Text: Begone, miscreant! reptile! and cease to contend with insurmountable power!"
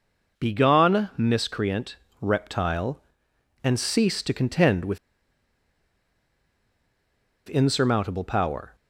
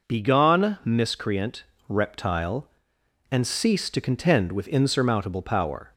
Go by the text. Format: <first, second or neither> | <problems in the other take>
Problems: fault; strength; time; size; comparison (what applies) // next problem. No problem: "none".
second | pauses between "with" and "insurmountable"; strong; at 4.9 s; 2.5 s long